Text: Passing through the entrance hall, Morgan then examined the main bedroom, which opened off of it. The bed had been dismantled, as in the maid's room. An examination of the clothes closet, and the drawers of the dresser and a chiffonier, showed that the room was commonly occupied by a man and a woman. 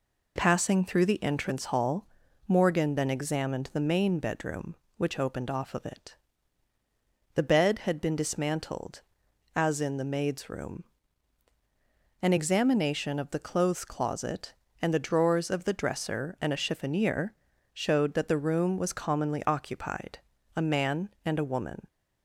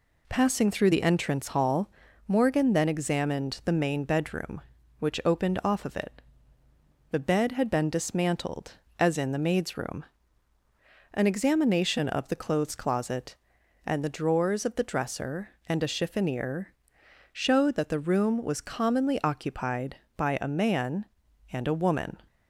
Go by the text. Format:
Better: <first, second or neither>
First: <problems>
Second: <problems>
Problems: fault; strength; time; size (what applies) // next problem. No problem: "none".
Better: second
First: skips "by"; at 20.3 s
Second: none